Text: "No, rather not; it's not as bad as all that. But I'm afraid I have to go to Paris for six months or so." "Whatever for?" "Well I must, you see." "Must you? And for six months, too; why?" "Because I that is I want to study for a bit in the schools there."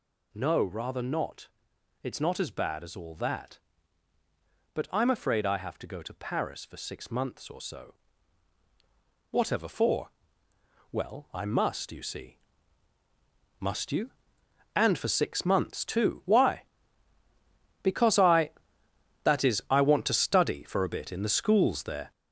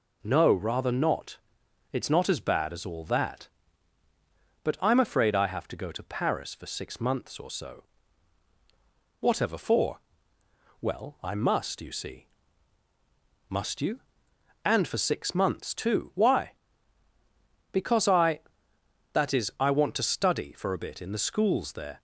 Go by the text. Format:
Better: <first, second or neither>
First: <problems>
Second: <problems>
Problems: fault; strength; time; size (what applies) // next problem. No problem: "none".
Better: second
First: gets louder; throughout; 7 dB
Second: none